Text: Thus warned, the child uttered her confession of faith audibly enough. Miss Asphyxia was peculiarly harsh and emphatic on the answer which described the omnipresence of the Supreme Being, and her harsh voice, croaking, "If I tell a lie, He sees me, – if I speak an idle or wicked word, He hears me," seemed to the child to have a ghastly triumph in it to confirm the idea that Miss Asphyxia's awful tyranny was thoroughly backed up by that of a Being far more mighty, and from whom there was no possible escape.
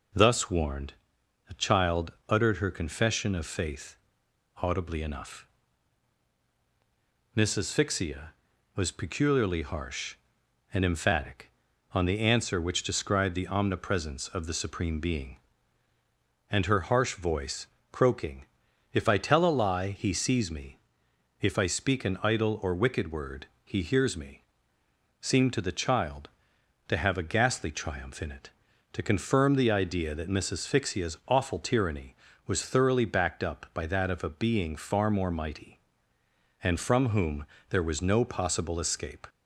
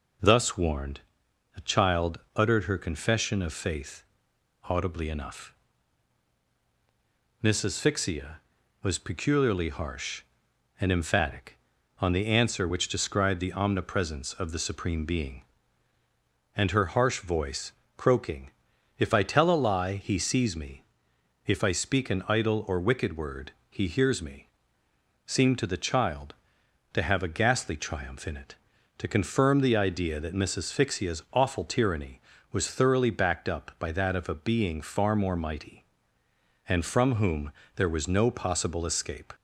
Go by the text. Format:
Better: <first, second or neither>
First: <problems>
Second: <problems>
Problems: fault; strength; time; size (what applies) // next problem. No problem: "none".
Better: neither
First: pauses between "child" and "uttered"; slight; at 2.1 s; 0.18 s long // pauses between "faith" and "audibly"; noticeable; at 3.9 s; 0.64 s long // pauses between "whom" and "there"; slight; at 37.4 s; 0.24 s long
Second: pauses between "child" and "uttered"; slight; at 2.1 s; 0.18 s long // pauses between "faith" and "audibly"; noticeable; at 4.0 s; 0.64 s long // pauses between "whom" and "there"; slight; at 37.5 s; 0.24 s long